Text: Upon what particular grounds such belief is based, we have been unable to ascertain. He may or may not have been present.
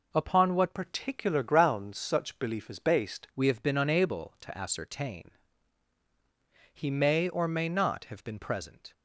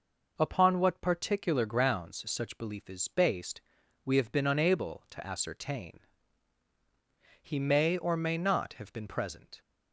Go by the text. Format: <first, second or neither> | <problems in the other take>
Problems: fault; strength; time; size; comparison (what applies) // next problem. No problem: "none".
second | changes voice from "particular" to "based"; from 0.7 to 3.2 s; 2.5 s long